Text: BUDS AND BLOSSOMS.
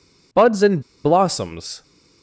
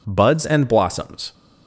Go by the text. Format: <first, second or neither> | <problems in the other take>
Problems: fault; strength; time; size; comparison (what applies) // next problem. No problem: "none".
second | pauses between "AND" and "BLOSSOMS"; slight; at 0.8 s; 0.22 s long